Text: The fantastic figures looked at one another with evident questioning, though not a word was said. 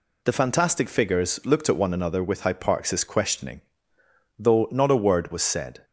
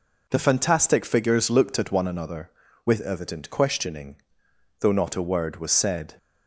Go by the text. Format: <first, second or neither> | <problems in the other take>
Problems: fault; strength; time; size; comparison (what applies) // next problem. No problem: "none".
second | says "hyparxis" for "evident"; at 2.4 s